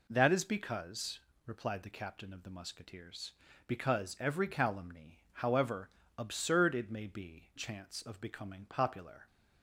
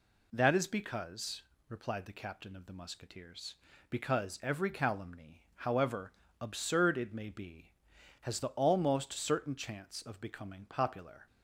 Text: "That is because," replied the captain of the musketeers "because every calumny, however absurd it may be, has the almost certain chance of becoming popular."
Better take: second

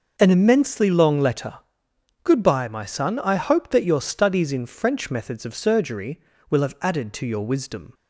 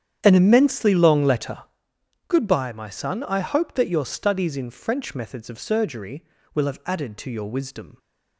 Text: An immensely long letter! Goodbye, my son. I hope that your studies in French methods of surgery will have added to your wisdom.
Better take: first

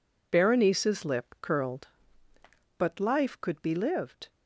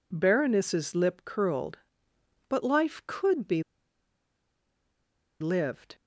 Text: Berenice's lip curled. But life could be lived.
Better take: first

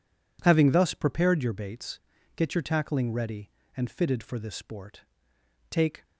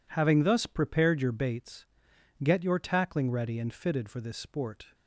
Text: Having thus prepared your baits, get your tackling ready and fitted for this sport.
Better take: second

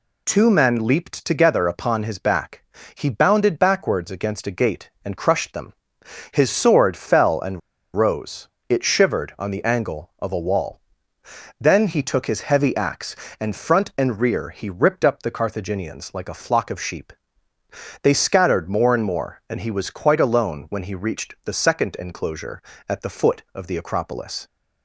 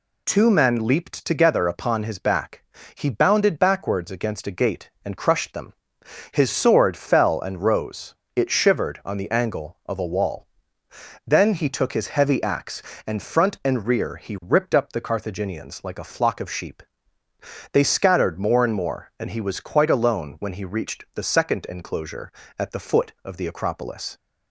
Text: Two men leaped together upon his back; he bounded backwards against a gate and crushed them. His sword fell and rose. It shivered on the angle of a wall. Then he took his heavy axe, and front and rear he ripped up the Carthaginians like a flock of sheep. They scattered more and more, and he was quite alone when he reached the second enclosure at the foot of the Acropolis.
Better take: second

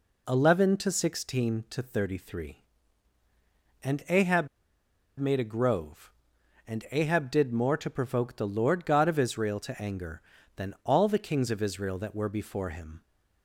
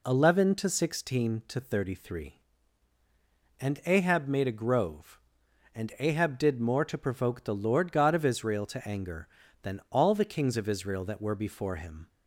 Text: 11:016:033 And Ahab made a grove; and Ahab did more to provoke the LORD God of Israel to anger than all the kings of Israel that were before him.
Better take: second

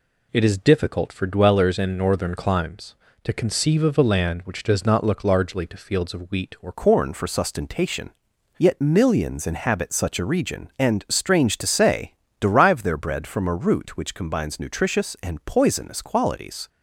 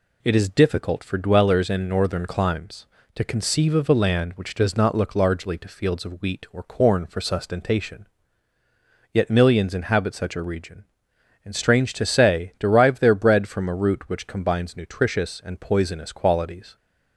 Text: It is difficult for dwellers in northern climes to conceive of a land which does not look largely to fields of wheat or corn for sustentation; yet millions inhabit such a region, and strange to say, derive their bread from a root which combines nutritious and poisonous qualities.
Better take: second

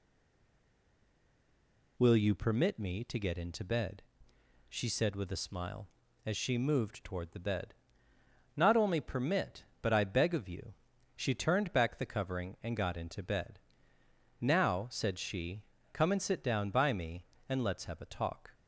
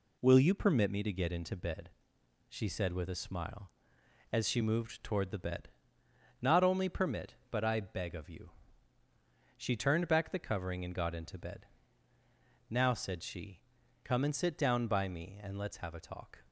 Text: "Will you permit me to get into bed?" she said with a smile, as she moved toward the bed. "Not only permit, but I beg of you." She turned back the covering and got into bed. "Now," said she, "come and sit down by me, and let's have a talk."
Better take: second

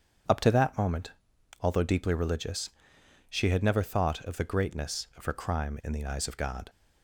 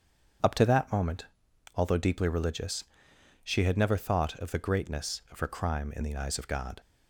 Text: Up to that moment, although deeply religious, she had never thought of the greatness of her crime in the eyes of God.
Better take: neither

